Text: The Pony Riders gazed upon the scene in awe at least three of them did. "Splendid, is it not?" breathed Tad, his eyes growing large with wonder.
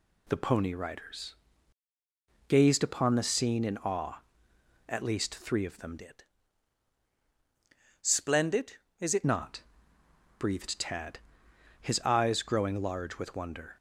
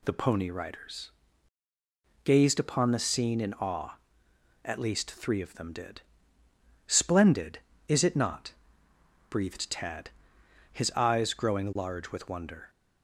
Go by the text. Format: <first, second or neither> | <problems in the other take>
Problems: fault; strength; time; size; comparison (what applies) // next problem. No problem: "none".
second | pauses between "Riders" and "gazed"; at 1.3 s; 1.1 s long; also in the second // changes voice from "did" to "it"; from 5.9 to 9.2 s; 3.3 s long